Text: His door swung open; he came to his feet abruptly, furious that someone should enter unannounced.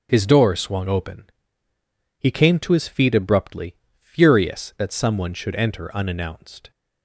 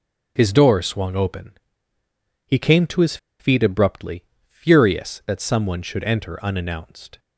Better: first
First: starts louder than the rest; until 1.1 s; 7 dB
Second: starts louder than the rest; until 1.3 s; 6 dB // pauses between "his" and "feet"; slight; at 3.1 s; 0.23 s long

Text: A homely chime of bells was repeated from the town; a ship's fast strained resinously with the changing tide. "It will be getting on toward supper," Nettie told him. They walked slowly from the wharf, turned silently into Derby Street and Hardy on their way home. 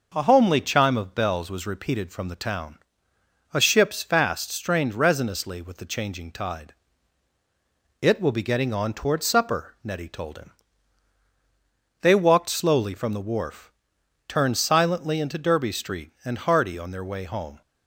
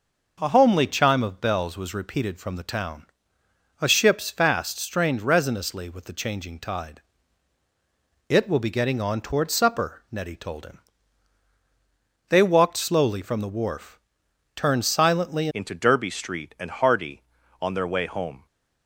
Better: first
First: none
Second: changes voice at "into"; from 15.5 s on; 2.9 s long

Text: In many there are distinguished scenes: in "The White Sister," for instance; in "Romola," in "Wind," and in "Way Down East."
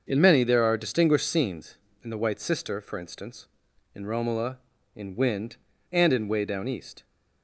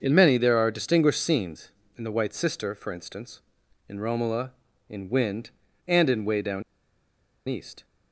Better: first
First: starts louder than the rest; until 1.0 s; 6.5 dB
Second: starts louder than the rest; until 1.0 s; 6.5 dB // pauses between "Down" and "East"; noticeable; at 6.6 s; 0.86 s long

